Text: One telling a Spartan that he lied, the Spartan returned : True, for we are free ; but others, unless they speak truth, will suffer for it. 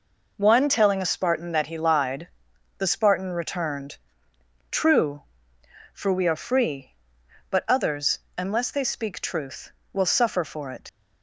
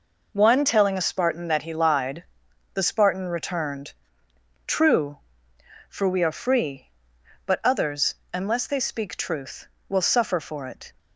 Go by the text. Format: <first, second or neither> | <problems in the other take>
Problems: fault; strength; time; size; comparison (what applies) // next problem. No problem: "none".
second | leaves "it" unfinished; at 10.8 s; 130 ms